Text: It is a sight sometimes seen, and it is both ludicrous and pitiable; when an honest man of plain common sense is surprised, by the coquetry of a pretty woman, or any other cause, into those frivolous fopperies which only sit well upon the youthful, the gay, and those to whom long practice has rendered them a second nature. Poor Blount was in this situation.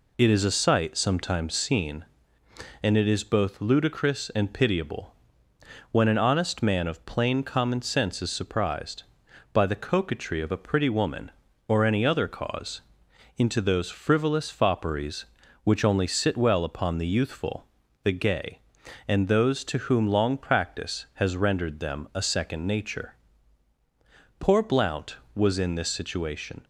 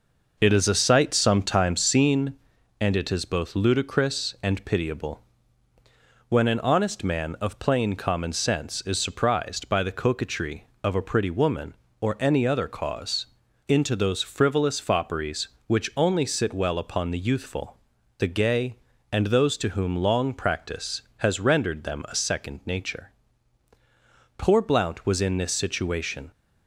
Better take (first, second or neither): first